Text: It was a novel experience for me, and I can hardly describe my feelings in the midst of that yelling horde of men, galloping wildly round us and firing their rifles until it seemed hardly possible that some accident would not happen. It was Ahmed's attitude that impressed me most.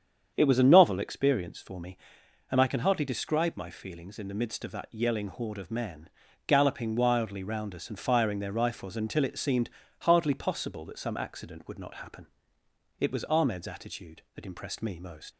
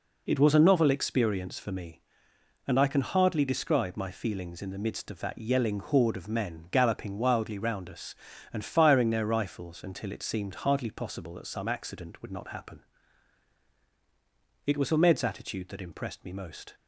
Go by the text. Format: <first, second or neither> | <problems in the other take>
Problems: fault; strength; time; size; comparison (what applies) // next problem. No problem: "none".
second | starts louder than the rest; strong; until 1.3 s; 7.5 dB // pauses between "seemed" and "hardly"; slight; at 9.6 s; 0.32 s long // leaves "most" unfinished; at 15.3 s; 75 ms